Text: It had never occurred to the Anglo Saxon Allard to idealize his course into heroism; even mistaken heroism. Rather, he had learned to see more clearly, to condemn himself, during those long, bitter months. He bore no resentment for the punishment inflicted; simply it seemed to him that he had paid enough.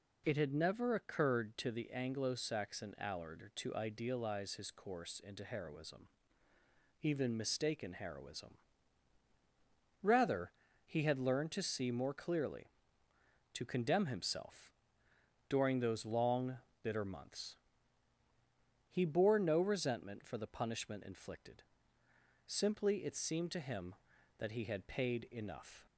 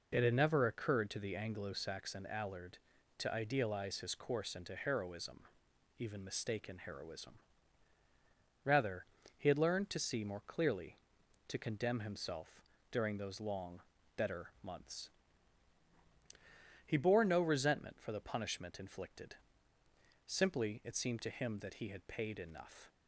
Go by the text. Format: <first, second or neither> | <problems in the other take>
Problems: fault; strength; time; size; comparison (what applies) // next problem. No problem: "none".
first | says "better" for "bitter"; at 14.1 s